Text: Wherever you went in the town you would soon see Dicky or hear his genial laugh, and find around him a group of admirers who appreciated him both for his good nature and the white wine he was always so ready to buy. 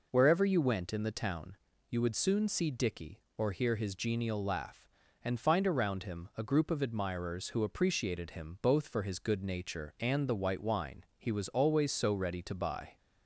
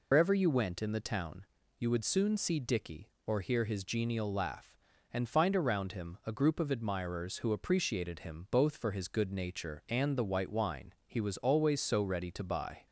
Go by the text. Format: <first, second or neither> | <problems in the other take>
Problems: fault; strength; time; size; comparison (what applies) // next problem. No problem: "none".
first | loses the start of "Wherever"; at 0.1 s; 120 ms // pauses between "town" and "you"; slight; at 1.4 s; 0.32 s long; slight in the first